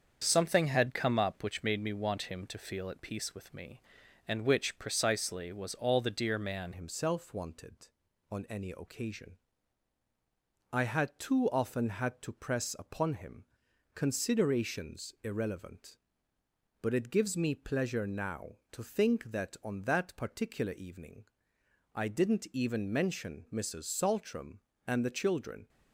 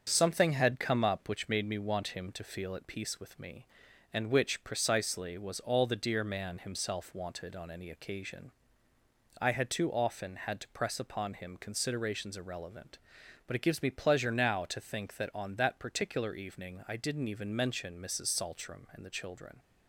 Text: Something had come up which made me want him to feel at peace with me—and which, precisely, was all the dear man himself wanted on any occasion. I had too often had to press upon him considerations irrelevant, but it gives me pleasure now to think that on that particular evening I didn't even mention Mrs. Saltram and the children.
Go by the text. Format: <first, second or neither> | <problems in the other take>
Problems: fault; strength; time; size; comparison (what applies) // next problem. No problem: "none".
second | starts louder than the rest; strong; until 1.2 s; 7 dB; strong in the second // changes voice at "himself"; from 6.7 s on; 18.9 s long // pauses between "him" and "considerations"; noticeable; at 13.4 s; 0.50 s long // pauses between "evening" and "I"; noticeable; at 21.2 s; 0.68 s long